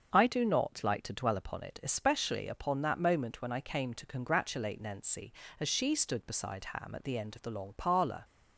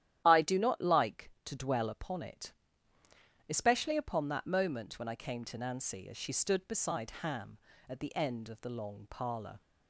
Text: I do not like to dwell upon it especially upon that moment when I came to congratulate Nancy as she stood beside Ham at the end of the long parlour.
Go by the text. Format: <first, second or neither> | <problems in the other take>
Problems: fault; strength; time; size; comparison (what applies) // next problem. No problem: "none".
first | starts louder than the rest; strong; until 1.2 s; 11.5 dB; also in the first // pauses between "it" and "especially"; noticeable; at 2.5 s; 0.96 s long // skips "congratulate"; at 5.5 s